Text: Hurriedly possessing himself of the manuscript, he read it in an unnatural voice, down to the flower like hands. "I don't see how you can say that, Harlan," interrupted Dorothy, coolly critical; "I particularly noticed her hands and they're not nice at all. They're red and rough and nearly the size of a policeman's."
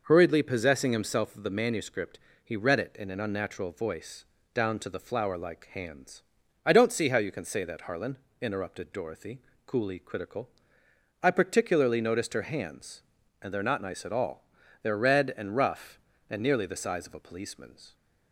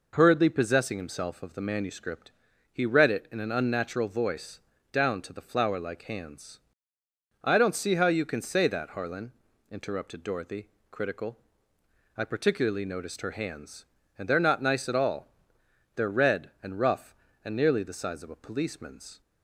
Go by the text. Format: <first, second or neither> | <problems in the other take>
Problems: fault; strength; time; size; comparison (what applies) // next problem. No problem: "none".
first | skips "coolly"; at 10.7 s